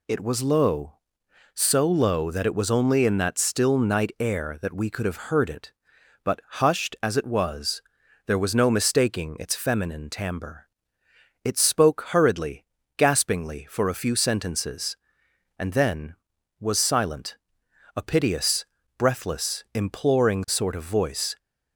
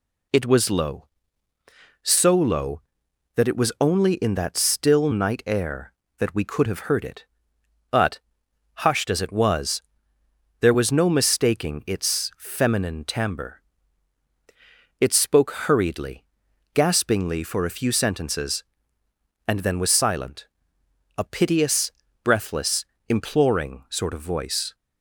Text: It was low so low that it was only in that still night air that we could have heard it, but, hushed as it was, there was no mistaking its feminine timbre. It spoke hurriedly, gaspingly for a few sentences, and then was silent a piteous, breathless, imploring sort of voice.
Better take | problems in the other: neither | pauses between "silent" and "a"; noticeable; the same in both

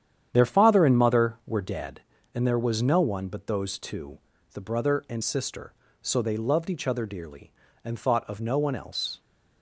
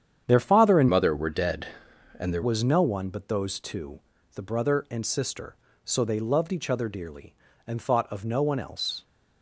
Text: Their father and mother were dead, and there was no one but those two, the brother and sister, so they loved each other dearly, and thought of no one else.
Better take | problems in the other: first | starts louder than the rest; strong; until 1.2 s; 8.5 dB; strong in the first // changes voice from "mother" to "there"; from 0.8 to 2.4 s; 1.6 s long

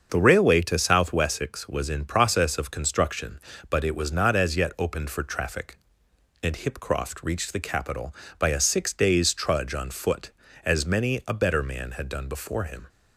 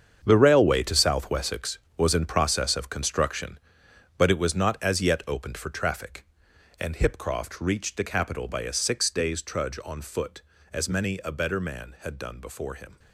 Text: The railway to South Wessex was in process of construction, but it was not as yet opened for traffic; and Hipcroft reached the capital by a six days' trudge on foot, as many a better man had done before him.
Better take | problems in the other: first | gets quieter; strong; throughout; 12 dB // starts louder than the rest; strong; until 1.2 s; 7.5 dB; also in the first

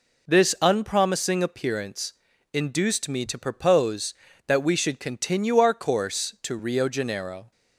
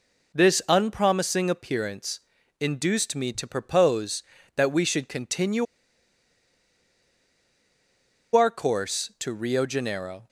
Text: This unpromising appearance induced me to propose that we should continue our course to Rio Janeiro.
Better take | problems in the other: first | pauses between "appearance" and "induced"; at 2.2 s; 0.40 s long; also in the first // pauses between "continue" and "our"; strong; at 5.6 s; 2.7 s long

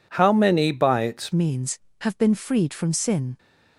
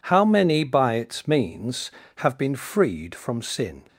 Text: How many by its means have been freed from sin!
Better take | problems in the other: second | changes voice at "means"; from 1.3 s on; 2.0 s long

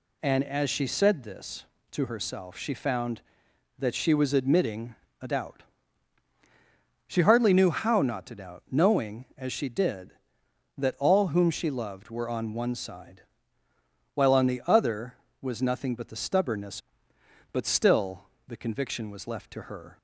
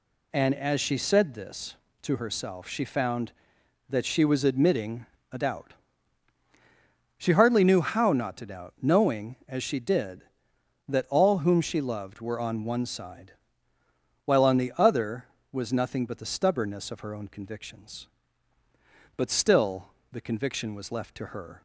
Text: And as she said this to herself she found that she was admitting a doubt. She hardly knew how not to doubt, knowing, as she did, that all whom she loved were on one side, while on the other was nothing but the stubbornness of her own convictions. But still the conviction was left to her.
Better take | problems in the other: second | pauses between "admitting" and "a"; slight; at 4.9 s; 0.28 s long; slight in the second // skips "of her own convictions"; at 17.1 s // pauses between "still" and "the"; slight; at 18.2 s; 0.22 s long; slight in the second

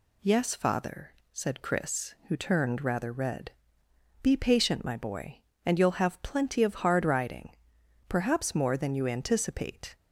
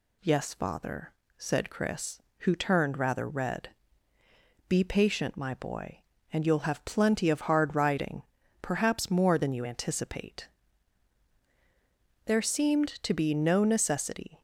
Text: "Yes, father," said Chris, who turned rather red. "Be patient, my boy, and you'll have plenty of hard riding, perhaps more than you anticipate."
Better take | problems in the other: first | goes on to say "There seemed to be no necessity"; strong; from 12.2 s on; 2.1 s long

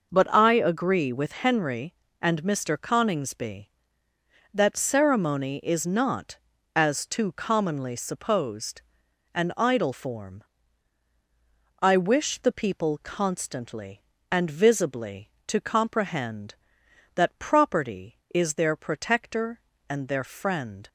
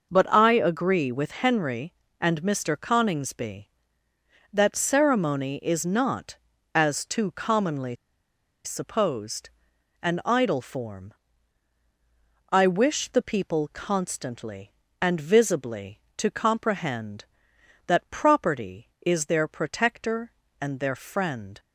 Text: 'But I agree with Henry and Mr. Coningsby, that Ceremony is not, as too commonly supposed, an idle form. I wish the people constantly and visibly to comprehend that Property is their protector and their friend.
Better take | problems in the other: first | pauses between "commonly" and "supposed"; noticeable; at 7.9 s; 0.70 s long

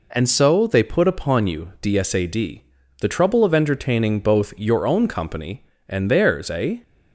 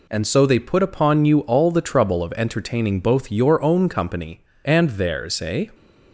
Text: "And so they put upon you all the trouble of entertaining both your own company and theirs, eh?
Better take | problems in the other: second | says "dsad" for "all"; at 1.8 s

